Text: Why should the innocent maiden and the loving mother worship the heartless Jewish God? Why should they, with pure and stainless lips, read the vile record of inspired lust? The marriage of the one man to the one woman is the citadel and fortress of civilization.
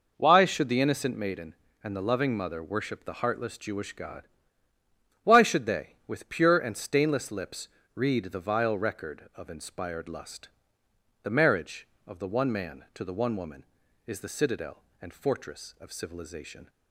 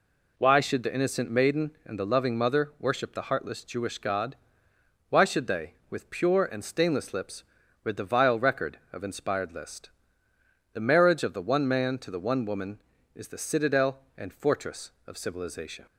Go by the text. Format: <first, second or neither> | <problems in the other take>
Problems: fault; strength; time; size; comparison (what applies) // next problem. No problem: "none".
first | says "list" for "lust"; at 9.5 s